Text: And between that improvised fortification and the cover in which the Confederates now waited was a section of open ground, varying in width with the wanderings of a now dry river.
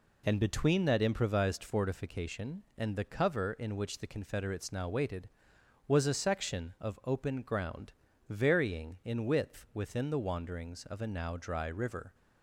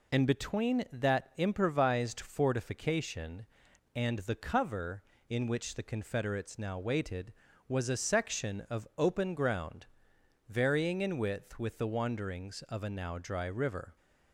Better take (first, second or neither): second